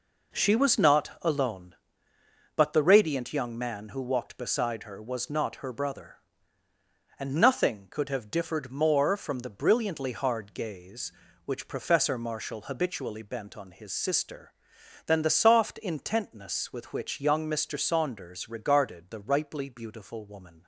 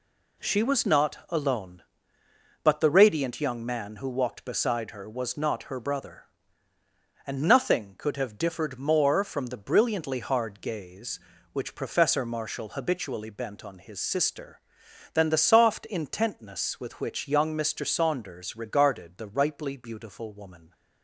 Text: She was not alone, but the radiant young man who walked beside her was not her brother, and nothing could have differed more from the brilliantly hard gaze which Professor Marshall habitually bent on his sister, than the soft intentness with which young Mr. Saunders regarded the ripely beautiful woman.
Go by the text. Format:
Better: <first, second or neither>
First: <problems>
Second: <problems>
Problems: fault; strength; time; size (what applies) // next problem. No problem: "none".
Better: second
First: starts louder than the rest; noticeable; until 1.4 s; 4.5 dB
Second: none